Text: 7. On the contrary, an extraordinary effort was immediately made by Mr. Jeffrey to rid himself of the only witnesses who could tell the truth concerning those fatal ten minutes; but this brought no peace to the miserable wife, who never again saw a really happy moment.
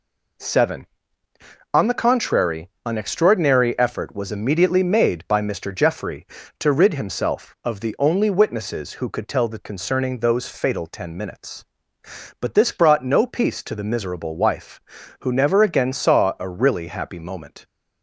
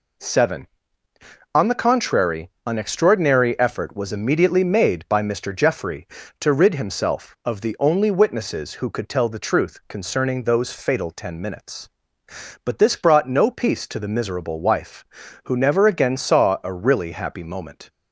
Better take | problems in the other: second | skips "truth"; at 9.6 s

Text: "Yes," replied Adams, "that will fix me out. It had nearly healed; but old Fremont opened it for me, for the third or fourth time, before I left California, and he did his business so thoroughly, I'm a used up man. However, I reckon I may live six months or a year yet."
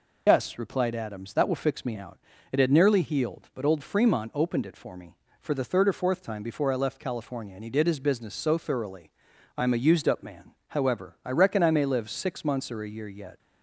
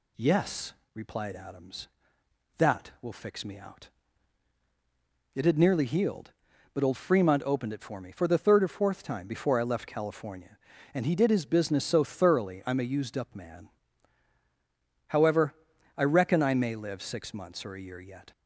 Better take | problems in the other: second | loses the start of "Yes"; at 0.2 s; 125 ms

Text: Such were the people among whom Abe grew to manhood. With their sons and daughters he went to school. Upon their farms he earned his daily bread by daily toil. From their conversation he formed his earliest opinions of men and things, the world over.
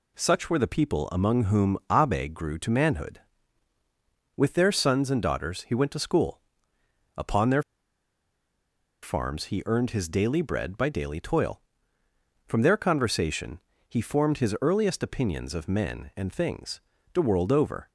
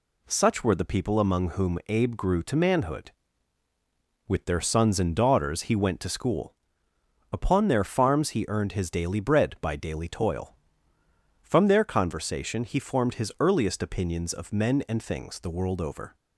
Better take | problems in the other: second | pauses between "their" and "farms"; strong; at 7.6 s; 1.4 s long // pauses between "conversation" and "he"; slight; at 13.6 s; 0.26 s long

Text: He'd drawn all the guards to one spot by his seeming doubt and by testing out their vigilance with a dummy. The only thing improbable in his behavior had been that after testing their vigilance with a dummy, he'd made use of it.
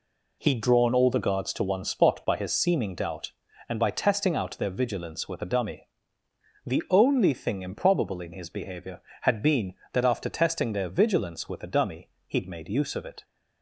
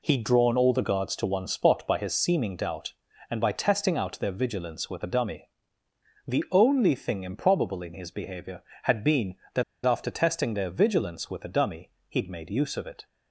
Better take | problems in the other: first | pauses between "that" and "after"; slight; at 9.6 s; 0.22 s long

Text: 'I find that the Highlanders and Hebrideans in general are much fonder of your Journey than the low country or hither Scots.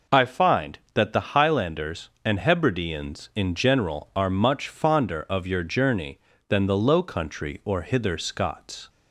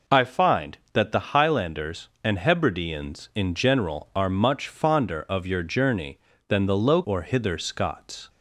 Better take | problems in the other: first | skips "country"; at 7.0 s

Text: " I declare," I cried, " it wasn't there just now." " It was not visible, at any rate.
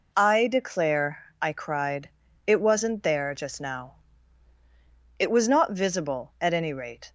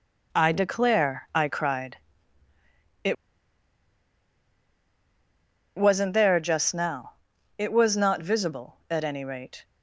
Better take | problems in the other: first | pauses between "it" and "wasn't"; strong; at 3.1 s; 2.6 s long

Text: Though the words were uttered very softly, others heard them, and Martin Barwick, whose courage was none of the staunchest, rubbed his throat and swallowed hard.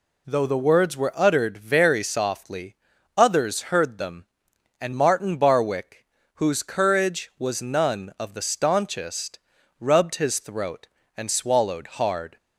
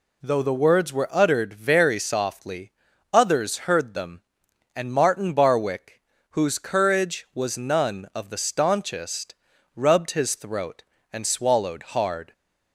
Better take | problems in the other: neither | none

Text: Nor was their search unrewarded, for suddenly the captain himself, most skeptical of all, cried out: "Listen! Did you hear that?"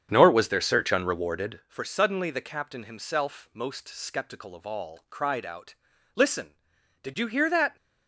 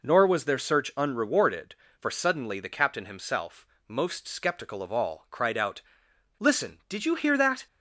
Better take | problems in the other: second | starts louder than the rest; strong; until 1.7 s; 8 dB

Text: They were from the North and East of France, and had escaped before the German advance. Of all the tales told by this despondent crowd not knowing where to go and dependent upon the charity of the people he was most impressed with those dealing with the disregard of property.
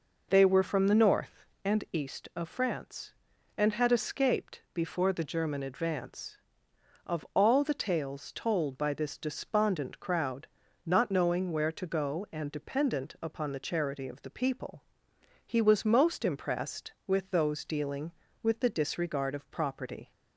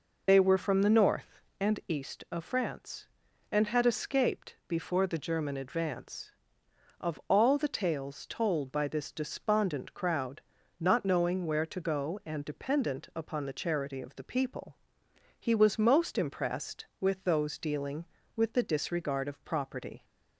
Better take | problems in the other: first | loses the start of "They"; at 0.2 s; 40 ms // pauses between "crowd" and "not"; at 10.4 s; 0.38 s long; also in the first // pauses between "people" and "he"; noticeable; at 14.7 s; 0.62 s long; noticeable in the first

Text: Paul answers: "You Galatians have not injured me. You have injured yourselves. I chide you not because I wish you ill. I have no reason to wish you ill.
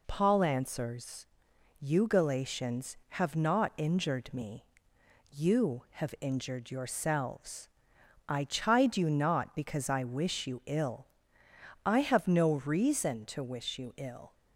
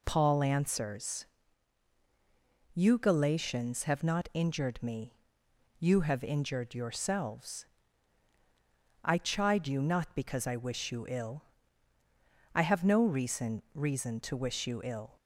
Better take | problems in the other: first | says "reason" twice; at 13.7 s

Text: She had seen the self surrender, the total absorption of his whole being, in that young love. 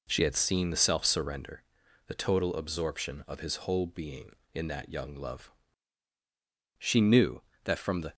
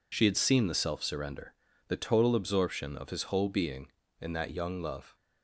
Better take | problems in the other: second | goes on to say "She knew that from the"; from 6.7 s on; 1.3 s long

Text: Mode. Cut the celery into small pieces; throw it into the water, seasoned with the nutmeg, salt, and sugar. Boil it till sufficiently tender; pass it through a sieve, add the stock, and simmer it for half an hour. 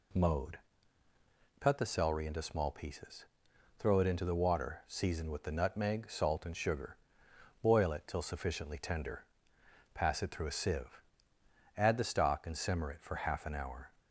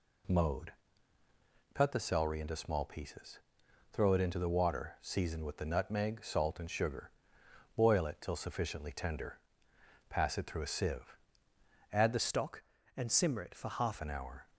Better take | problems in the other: first | changes voice from "stock" to "half"; from 12.1 to 13.9 s; 1.8 s long

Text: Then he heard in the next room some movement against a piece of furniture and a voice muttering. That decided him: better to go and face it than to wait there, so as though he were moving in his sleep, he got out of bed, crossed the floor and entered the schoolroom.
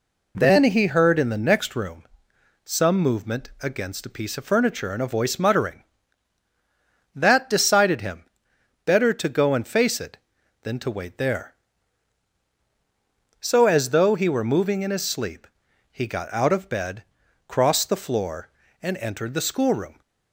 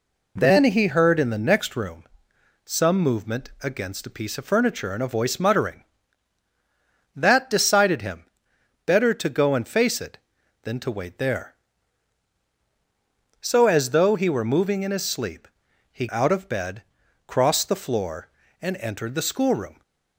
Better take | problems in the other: first | pauses between "room" and "some"; noticeable; at 2.0 s; 0.62 s long; noticeable in the first // skips "got"; at 16.0 s

